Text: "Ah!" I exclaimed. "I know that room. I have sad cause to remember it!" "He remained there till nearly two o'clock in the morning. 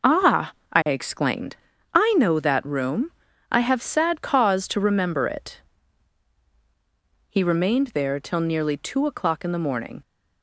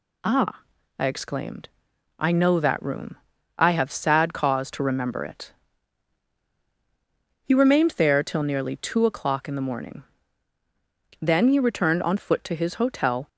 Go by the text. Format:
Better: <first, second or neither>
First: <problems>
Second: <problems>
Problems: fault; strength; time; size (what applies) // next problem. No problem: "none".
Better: first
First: none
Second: goes on to say "Then he returned on foot to his hotel"; strong; from 11.1 s on; 2.0 s long